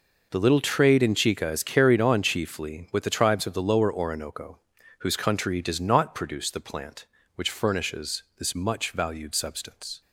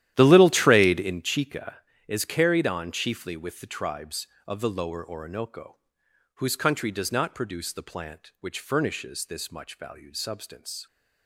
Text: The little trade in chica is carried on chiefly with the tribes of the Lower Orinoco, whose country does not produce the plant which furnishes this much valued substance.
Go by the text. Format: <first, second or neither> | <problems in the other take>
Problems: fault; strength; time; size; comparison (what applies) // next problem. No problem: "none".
first | starts louder than the rest; strong; until 1.2 s; 12.5 dB